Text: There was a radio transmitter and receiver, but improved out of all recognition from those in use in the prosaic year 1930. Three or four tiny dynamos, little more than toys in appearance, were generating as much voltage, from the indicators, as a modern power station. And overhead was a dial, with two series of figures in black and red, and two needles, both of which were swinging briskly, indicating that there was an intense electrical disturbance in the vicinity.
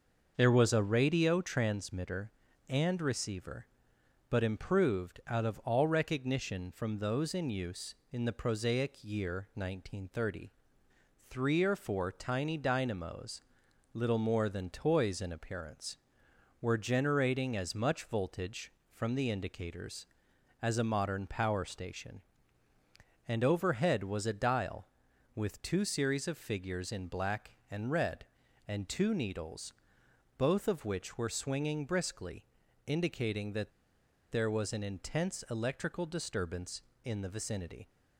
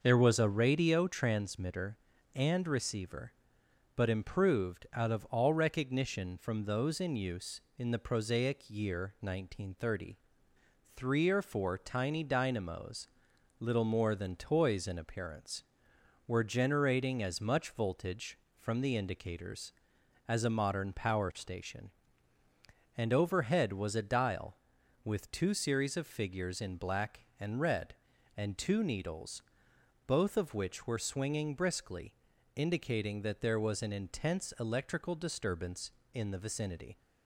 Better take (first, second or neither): second